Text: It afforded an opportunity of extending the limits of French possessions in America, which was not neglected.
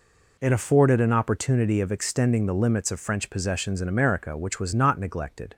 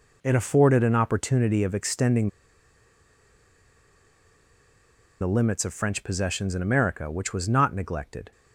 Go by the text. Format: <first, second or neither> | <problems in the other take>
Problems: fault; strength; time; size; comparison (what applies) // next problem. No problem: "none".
first | pauses between "extending" and "the"; strong; at 2.2 s; 2.9 s long